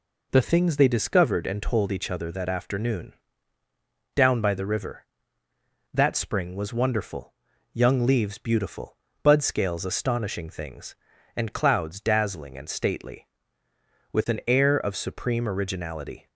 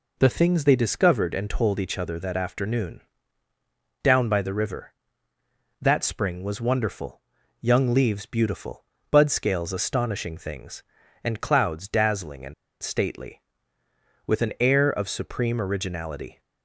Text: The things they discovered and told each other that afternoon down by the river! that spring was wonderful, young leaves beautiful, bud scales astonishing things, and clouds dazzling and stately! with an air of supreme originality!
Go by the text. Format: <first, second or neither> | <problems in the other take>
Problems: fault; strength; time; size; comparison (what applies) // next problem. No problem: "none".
first | pauses between "afternoon" and "down"; at 3.0 s; 1.0 s long; also in the first // pauses between "and" and "stately"; slight; at 12.5 s; 0.29 s long